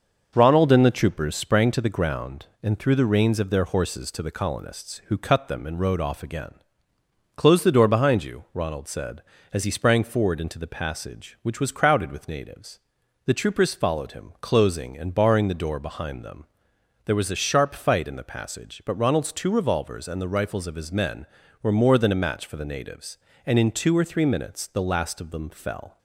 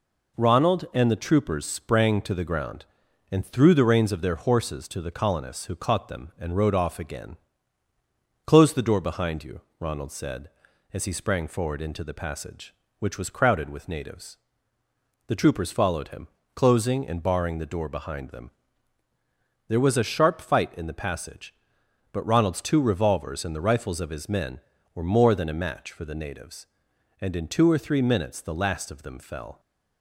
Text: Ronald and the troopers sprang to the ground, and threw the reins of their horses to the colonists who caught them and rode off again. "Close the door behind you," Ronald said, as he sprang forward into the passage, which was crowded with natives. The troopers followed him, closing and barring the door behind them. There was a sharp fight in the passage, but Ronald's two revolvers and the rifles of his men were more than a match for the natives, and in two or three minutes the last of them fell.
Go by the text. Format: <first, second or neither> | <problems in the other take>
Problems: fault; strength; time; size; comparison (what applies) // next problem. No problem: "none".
second | says "cut" for "caught"; at 5.1 s